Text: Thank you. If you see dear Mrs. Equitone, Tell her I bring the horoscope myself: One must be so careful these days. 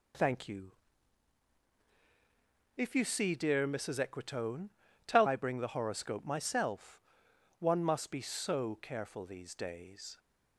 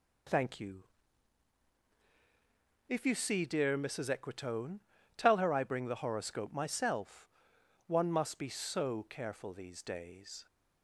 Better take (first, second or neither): second